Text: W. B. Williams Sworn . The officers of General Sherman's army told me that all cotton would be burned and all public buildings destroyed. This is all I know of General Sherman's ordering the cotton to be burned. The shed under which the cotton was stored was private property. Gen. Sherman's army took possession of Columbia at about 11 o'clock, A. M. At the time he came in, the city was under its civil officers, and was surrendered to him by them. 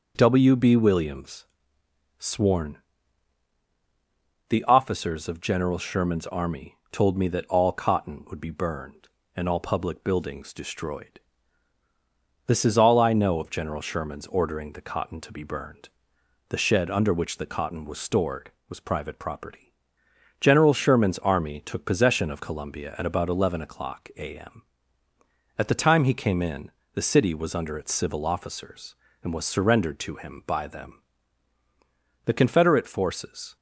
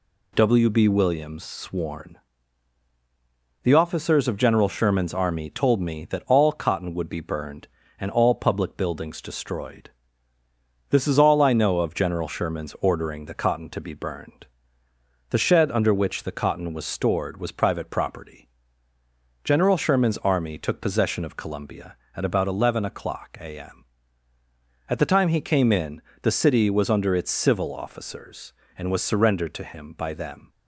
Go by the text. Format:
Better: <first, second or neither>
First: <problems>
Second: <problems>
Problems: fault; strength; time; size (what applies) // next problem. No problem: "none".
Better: second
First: pauses between "Williams" and "Sworn"; noticeable; at 1.4 s; 0.74 s long // goes on to say "The Confederate forces"; noticeable; from 32.2 s on; 1.3 s long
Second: none